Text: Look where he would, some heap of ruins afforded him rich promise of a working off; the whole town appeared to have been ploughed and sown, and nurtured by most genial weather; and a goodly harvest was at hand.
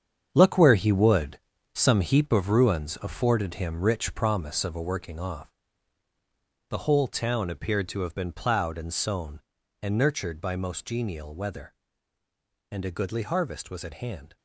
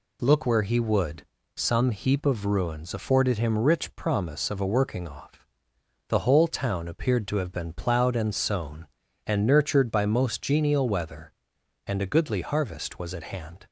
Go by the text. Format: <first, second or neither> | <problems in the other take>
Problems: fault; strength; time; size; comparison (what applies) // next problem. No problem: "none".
second | gets quieter; strong; throughout; 10 dB